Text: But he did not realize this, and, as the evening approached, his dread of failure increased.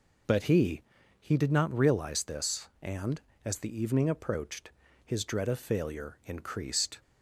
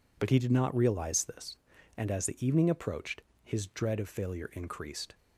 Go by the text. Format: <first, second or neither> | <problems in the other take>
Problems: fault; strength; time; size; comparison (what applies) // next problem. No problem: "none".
second | says "he" twice; at 1.2 s